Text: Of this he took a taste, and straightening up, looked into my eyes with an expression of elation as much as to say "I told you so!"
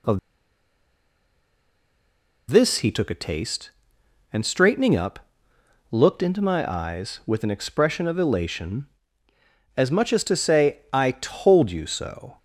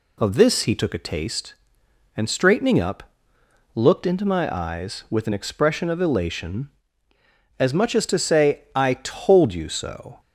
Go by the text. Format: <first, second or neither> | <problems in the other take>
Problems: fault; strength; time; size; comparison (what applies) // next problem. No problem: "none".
second | pauses between "Of" and "this"; strong; at 0.1 s; 2.3 s long